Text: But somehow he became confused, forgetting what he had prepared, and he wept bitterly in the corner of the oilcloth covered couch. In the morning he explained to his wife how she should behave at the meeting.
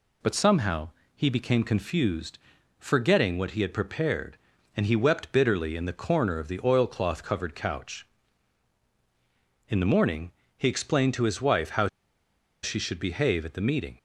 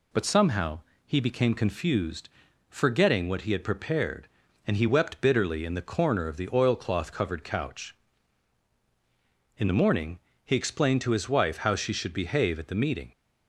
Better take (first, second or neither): second